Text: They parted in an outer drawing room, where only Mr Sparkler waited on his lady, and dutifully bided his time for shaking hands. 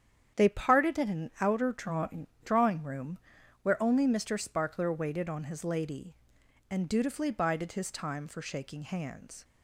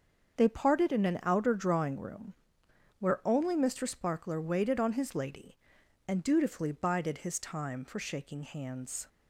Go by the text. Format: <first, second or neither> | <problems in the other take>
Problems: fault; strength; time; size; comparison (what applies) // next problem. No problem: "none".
second | starts louder than the rest; strong; until 1.4 s; 9 dB; also in the second // says "drawing" twice; at 2.4 s